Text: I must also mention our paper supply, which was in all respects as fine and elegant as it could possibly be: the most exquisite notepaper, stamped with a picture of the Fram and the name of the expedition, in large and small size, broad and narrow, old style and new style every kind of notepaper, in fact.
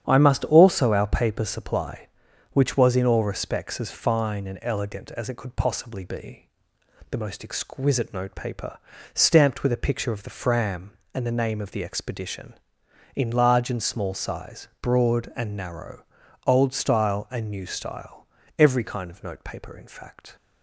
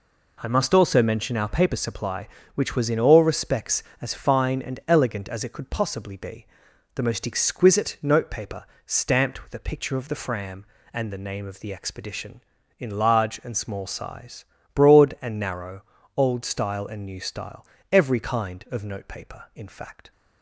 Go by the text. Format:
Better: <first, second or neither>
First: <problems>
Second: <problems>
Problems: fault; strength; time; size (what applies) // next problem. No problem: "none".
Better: second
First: starts louder than the rest; strong; until 1.1 s; 9 dB // skips "mention"; at 0.9 s // pauses between "style" and "every"; slight; at 18.2 s; 0.32 s long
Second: pauses between "style" and "every"; slight; at 17.6 s; 0.24 s long